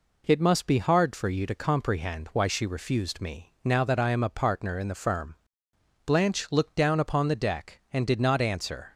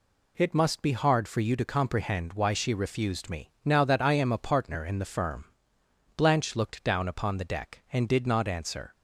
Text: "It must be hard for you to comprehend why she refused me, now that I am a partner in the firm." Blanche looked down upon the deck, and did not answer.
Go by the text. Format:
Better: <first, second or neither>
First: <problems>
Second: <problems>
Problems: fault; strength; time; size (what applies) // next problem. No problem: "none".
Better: neither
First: none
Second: none